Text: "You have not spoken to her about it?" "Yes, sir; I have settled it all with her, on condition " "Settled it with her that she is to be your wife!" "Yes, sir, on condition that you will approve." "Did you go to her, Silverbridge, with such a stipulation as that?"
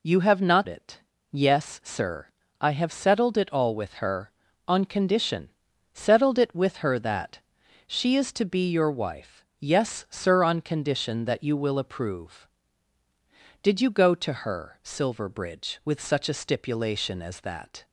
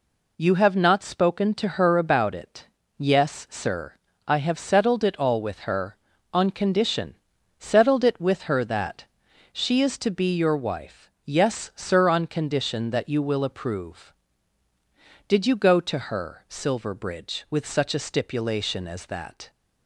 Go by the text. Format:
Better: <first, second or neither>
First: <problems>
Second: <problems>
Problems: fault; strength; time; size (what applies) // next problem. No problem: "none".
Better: second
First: skips "spoken to her about"; at 0.6 s // pauses between "that" and "she"; noticeable; at 7.3 s; 0.48 s long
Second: pauses between "that" and "she"; noticeable; at 9.0 s; 0.48 s long